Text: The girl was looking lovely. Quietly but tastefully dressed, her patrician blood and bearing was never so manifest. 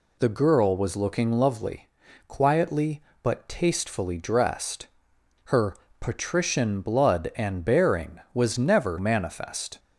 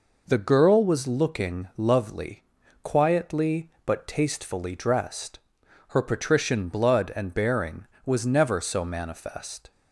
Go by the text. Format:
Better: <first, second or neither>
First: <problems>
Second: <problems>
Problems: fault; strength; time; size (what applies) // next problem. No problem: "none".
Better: second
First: pauses between "her" and "patrician"; slight; at 5.7 s; 0.24 s long // skips "so"; at 8.9 s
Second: none